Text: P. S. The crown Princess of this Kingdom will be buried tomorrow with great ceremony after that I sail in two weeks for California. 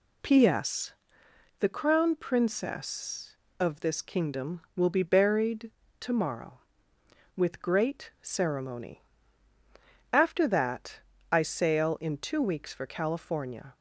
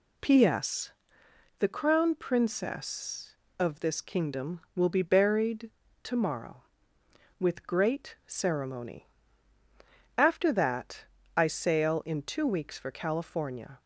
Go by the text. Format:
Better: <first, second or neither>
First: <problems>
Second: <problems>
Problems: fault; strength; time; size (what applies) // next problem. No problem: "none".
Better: neither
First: pauses between "buried" and "tomorrow"; slight; at 5.7 s; 0.28 s long // pauses between "ceremony" and "after"; at 9.0 s; 1.1 s long // pauses between "that" and "I"; slight; at 10.9 s; 0.32 s long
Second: pauses between "buried" and "tomorrow"; slight; at 5.7 s; 0.31 s long // pauses between "ceremony" and "after"; at 9.0 s; 1.1 s long // pauses between "that" and "I"; slight; at 11.0 s; 0.32 s long